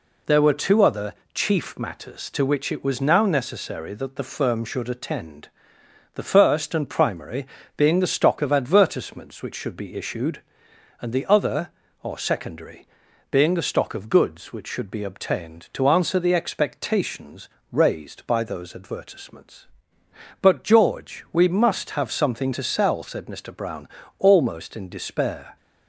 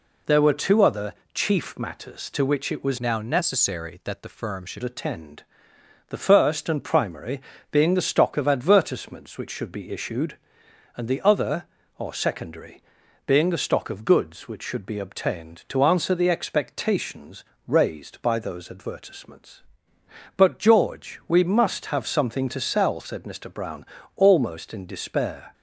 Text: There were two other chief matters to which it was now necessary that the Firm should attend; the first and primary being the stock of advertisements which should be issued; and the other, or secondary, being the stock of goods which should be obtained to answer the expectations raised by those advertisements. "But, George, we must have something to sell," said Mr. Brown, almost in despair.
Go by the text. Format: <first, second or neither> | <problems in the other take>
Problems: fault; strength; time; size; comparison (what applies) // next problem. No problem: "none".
first | pauses between "other" and "chief"; slight; at 1.1 s; 0.20 s long; slight in the first // changes voice from "now" to "should"; from 3.0 to 4.8 s; 1.8 s long // pauses between "primary" and "being"; slight; at 7.3 s; 0.32 s long; slight in the first // pauses between "expectations" and "raised"; slight; at 17.4 s; 0.24 s long; slight in the first